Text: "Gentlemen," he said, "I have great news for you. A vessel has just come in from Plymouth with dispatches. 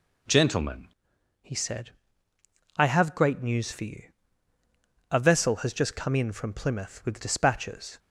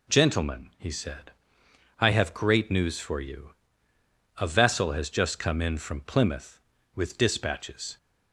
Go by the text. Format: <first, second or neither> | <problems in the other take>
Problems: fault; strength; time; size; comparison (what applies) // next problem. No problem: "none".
second | changes voice at "he"; from 1.4 s on; 6.5 s long